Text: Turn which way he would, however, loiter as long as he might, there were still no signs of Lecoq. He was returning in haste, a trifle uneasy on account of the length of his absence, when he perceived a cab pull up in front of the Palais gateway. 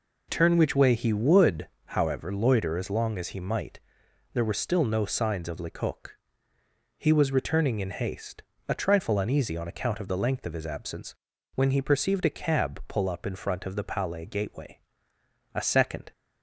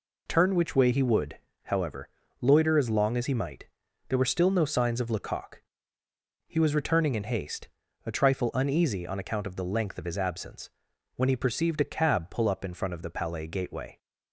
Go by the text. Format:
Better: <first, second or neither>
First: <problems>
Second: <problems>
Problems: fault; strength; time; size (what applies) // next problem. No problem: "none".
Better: second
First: goes on to say "A second"; from 15.5 s on; 0.58 s long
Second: none